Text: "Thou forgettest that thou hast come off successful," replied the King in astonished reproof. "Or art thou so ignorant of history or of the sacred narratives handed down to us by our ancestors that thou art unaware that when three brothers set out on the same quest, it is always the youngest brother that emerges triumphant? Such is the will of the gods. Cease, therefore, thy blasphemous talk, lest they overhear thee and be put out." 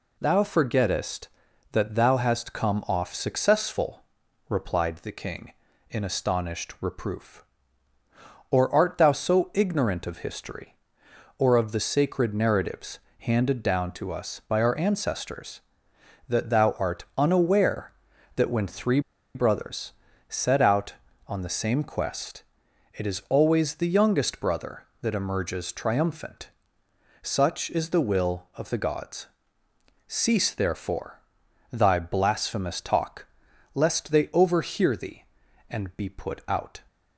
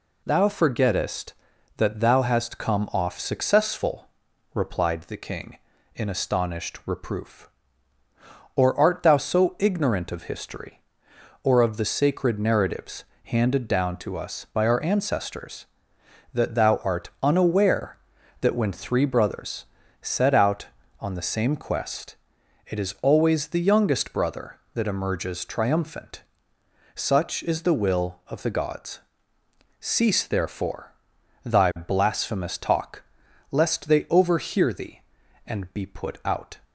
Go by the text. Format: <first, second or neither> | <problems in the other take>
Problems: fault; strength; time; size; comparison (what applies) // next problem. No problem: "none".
second | pauses between "narratives" and "handed"; slight; at 12.9 s; 0.22 s long; slight in the second // pauses between "three" and "brothers"; slight; at 18.9 s; 0.35 s long // pauses between "brothers" and "set"; slight; at 19.9 s; 0.36 s long; slight in the second